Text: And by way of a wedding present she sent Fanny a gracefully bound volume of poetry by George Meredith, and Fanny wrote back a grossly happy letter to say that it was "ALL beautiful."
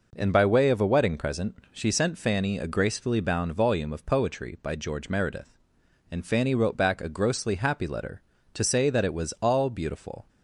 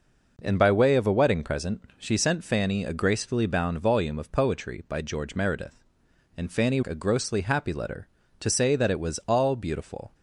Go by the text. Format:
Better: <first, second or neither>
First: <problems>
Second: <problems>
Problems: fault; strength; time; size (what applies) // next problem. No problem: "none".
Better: first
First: none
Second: skips "wrote back"; at 6.8 s